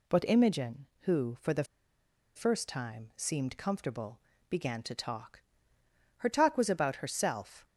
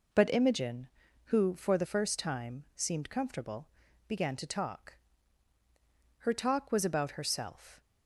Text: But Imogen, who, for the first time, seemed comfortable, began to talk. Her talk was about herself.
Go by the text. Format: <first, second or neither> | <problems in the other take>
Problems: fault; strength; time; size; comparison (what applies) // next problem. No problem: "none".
second | pauses between "the" and "first"; noticeable; at 1.6 s; 0.72 s long